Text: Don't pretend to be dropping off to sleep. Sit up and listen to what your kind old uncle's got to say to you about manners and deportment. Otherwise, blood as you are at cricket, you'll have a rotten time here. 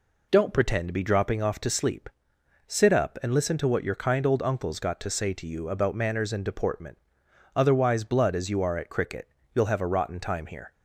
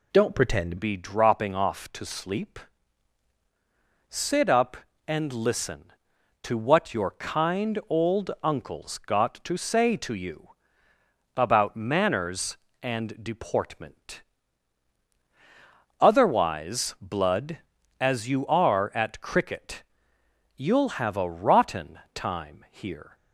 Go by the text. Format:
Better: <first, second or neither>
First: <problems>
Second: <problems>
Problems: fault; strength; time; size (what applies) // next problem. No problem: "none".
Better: first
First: none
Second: changes voice at "be"; from 0.7 s on; 22.4 s long // pauses between "you" and "about"; noticeable; at 10.4 s; 0.88 s long // pauses between "rotten" and "time"; slight; at 21.9 s; 0.16 s long